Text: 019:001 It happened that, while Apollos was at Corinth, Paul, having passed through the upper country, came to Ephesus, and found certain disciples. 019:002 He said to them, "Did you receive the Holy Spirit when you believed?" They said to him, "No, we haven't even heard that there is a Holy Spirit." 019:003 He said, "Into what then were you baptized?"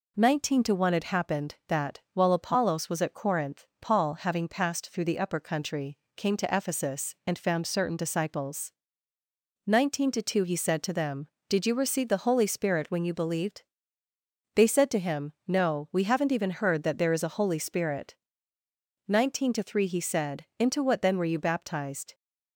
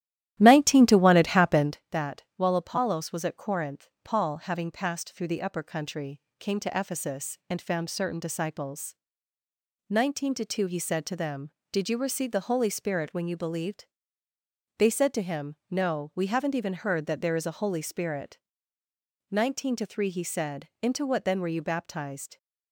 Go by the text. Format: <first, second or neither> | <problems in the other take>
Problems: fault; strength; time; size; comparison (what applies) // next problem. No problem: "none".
first | starts louder than the rest; strong; until 1.8 s; 13 dB